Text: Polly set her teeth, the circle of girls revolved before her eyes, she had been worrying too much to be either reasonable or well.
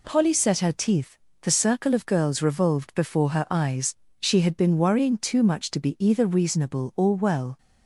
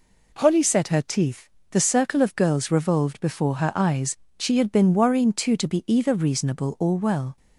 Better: first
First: none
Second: skips "much"; at 5.5 s

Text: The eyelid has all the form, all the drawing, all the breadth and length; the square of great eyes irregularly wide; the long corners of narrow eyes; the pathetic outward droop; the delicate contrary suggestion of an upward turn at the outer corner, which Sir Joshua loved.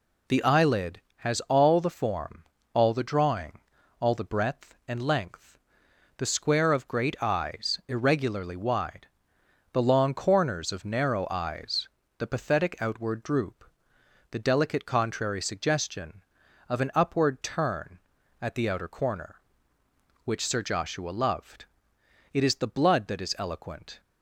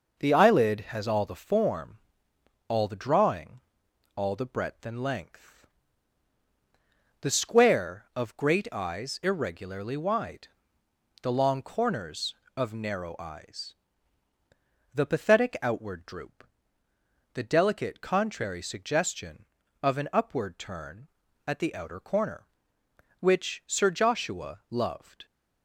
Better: second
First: goes on to say "It is the blood that is eloquent"; strong; from 22.3 s on; 1.6 s long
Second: none

